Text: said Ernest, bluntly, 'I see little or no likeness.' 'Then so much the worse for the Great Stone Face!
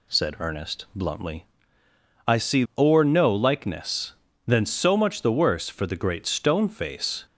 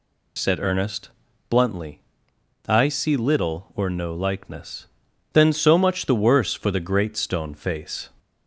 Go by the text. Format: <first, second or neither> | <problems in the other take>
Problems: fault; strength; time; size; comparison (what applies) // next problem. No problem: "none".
second | skips "little"; at 2.7 s